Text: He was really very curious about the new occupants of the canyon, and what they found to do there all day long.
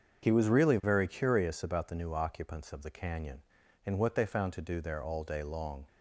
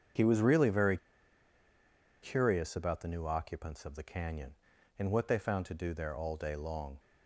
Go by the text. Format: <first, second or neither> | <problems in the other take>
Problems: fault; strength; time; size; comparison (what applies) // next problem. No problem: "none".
first | starts louder than the rest; until 2.4 s; 7 dB; also in the first // pauses between "very" and "curious"; strong; at 0.9 s; 1.2 s long